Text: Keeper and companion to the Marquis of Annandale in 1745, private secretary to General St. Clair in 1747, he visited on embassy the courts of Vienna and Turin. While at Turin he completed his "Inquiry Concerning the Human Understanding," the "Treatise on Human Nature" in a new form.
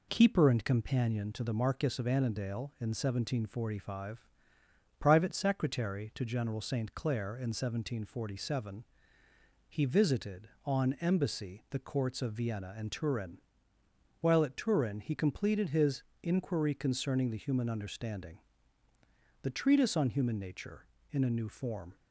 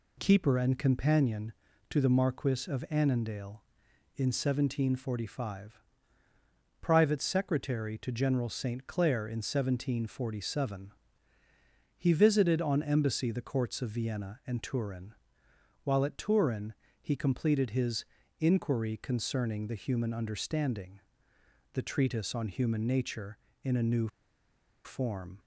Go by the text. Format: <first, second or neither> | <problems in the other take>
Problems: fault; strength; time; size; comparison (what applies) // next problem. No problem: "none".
first | pauses between "Turin" and "he"; slight; at 16.7 s; 0.26 s long // pauses between "his" and "Inquiry"; slight; at 18.0 s; 0.36 s long; slight in the first // pauses between "new" and "form"; noticeable; at 24.0 s; 0.76 s long